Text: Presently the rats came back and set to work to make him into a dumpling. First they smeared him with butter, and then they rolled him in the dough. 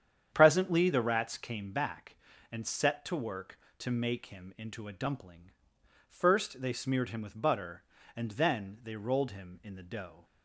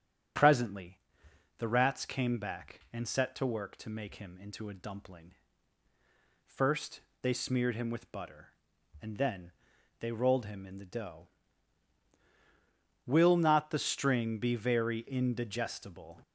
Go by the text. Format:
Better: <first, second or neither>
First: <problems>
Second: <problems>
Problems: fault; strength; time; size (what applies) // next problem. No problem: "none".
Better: first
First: starts louder than the rest; strong; until 1.3 s; 8.5 dB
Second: starts louder than the rest; strong; until 1.9 s; 8 dB // pauses between "Presently" and "the"; noticeable; at 0.9 s; 0.58 s long // pauses between "First" and "they"; slight; at 7.0 s; 0.22 s long // pauses between "then" and "they"; noticeable; at 9.5 s; 0.48 s long // goes on to say "Will not the string be very indigestible"; strong; from 13.0 s on; 3.1 s long